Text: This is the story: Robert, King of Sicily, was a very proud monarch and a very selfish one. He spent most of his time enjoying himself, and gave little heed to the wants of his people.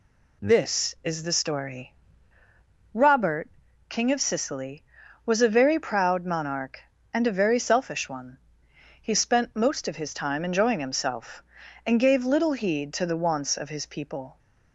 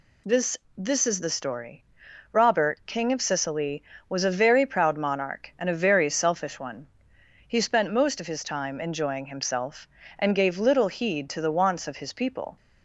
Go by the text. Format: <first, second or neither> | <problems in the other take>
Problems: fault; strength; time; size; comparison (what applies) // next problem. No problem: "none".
first | says "This" twice; at 0.7 s